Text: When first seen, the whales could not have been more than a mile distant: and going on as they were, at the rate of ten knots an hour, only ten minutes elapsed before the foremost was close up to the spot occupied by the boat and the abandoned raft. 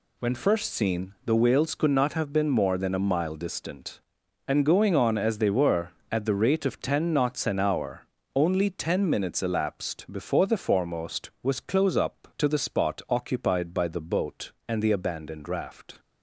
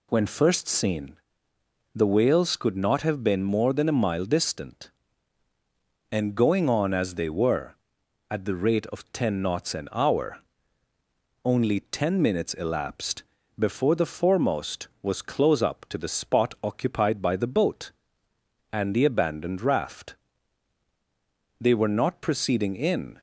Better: first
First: none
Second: pauses between "elapsed" and "before"; at 13.2 s; 0.38 s long // goes on to say "They were not proceeding in"; from 21.5 s on; 1.6 s long

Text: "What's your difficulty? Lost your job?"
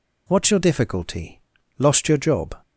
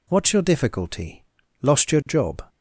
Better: neither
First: none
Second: none

